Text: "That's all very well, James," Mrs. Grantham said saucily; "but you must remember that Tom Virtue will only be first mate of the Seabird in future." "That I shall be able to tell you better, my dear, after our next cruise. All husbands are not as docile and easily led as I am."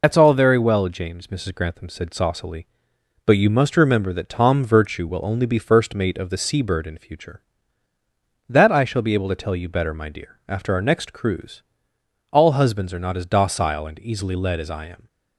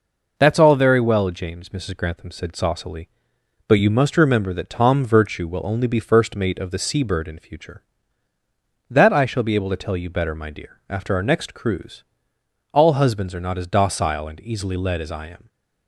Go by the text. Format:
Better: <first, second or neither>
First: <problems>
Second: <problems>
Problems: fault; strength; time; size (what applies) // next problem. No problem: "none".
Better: second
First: loses the start of "That's"; at 0.0 s; 80 ms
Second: none